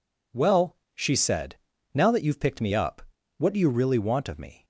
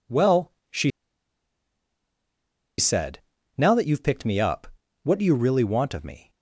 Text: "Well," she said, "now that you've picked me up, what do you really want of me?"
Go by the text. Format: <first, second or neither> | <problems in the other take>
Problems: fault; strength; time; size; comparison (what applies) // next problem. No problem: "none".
first | pauses between "she" and "said"; strong; at 0.8 s; 1.8 s long